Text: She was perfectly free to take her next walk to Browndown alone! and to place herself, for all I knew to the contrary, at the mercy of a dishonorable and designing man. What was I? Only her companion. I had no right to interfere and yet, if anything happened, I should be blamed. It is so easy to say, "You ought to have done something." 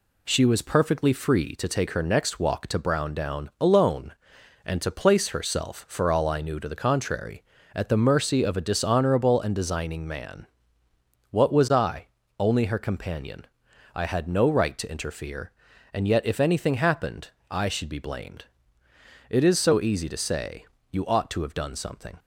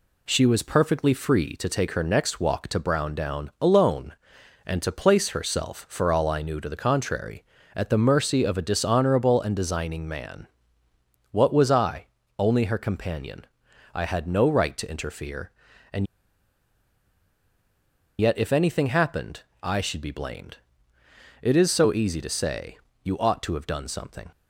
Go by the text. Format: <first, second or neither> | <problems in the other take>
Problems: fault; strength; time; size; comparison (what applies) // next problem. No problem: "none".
first | pauses between "and" and "yet"; strong; at 16.0 s; 2.1 s long